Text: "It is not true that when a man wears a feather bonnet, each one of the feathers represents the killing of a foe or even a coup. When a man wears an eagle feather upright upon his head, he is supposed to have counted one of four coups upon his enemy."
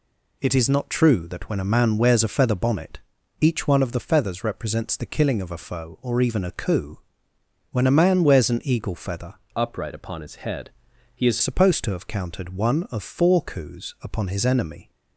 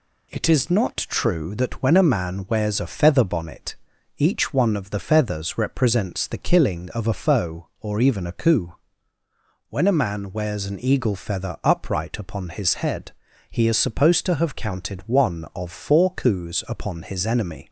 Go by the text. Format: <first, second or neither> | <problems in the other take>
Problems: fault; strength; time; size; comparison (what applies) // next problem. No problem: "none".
second | changes voice from "upright" to "is"; from 9.5 to 11.3 s; 1.8 s long